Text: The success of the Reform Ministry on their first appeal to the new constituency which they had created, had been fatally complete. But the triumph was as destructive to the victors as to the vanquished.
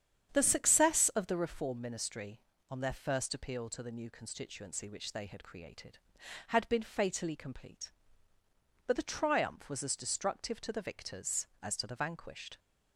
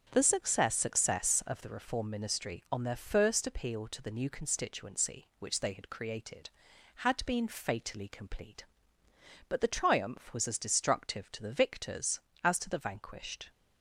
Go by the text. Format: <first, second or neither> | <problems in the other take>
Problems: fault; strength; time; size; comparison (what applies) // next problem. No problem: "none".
first | starts louder than the rest; strong; until 1.1 s; 7.5 dB; strong in the first // says "success" twice; at 0.7 s